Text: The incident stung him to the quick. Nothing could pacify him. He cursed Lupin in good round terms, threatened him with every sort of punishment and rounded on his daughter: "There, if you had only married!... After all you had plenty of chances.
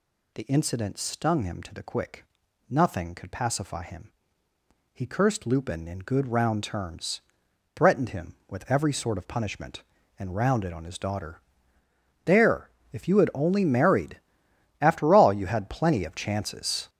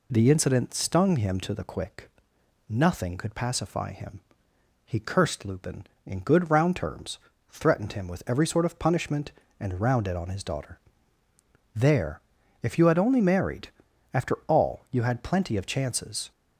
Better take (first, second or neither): second